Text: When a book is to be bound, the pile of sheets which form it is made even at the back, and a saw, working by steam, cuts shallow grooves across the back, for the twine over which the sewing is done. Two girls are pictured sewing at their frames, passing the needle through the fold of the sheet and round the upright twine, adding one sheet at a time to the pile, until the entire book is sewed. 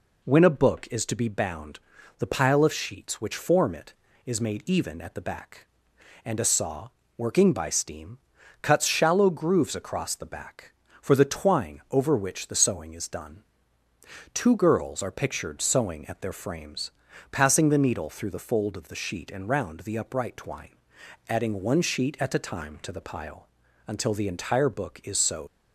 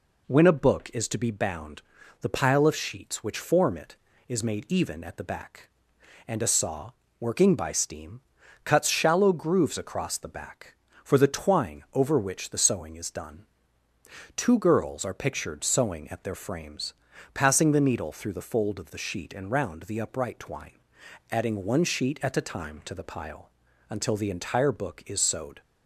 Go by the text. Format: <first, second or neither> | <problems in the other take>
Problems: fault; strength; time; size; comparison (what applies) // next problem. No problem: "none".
second | leaves "sewed" unfinished; at 25.4 s; 105 ms